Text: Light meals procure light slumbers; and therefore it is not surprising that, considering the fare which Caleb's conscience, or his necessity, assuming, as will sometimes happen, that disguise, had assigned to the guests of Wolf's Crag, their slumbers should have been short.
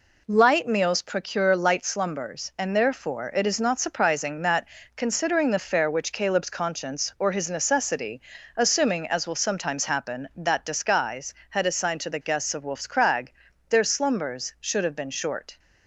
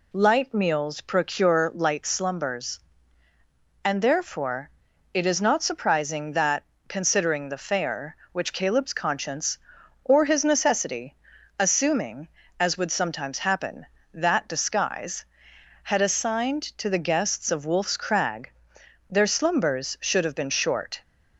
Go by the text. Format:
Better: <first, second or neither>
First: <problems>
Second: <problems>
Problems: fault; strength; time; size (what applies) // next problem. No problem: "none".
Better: first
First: none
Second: pauses between "therefore" and "it"; at 4.6 s; 0.44 s long // says "would" for "will"; at 12.7 s